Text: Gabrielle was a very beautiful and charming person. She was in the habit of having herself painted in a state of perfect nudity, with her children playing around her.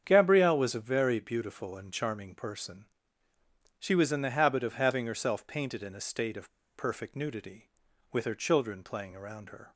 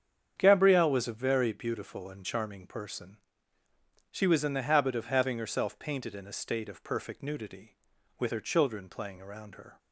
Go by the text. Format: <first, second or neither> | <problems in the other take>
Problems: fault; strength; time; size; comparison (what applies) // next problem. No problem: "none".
second | starts louder than the rest; strong; until 1.0 s; 8 dB; strong in the second // pauses between "of" and "perfect"; slight; at 6.4 s; 0.27 s long